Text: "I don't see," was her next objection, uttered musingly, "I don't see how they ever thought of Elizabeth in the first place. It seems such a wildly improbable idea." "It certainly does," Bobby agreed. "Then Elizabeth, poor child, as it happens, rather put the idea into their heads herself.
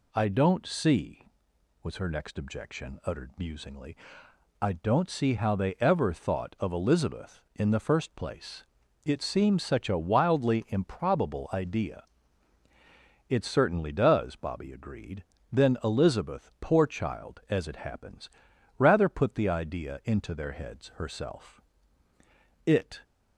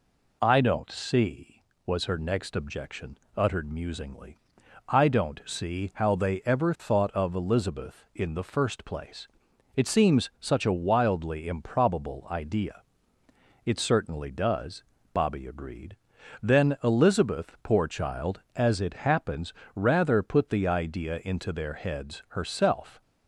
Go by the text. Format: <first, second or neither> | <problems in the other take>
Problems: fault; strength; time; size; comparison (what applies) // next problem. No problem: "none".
second | goes on to say "It"; slight; from 22.6 s on; 0.38 s long